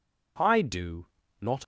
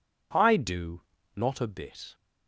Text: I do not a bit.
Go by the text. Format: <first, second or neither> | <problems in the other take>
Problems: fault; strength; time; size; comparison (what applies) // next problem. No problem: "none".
second | pauses between "do" and "not"; slight; at 1.0 s; 0.34 s long; slight in the second // stops before "a bit"; at 1.6 s